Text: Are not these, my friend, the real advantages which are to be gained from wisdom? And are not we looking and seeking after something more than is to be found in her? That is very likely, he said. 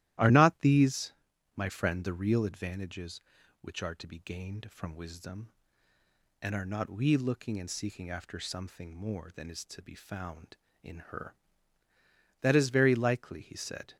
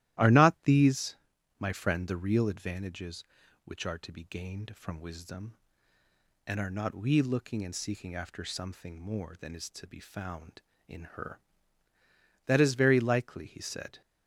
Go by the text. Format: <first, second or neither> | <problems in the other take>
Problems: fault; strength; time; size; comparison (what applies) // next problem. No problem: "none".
neither | starts louder than the rest; strong; the same in both